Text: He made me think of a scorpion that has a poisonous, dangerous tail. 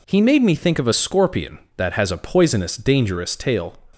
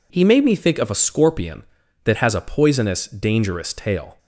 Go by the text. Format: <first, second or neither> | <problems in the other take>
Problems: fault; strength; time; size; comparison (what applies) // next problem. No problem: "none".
neither | none